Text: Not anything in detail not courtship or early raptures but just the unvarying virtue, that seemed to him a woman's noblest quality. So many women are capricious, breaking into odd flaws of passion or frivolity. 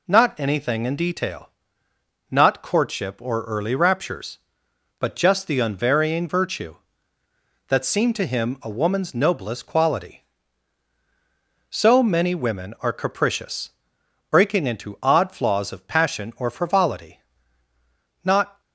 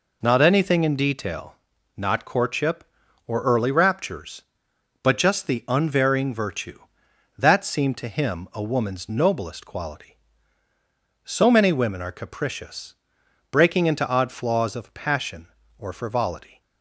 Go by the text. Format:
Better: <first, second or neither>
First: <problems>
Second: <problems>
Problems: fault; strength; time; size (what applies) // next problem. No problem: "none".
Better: second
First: pauses between "detail" and "not"; noticeable; at 1.4 s; 0.86 s long // goes on to say "Not"; slight; from 18.2 s on; 0.36 s long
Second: pauses between "detail" and "not"; at 1.5 s; 0.42 s long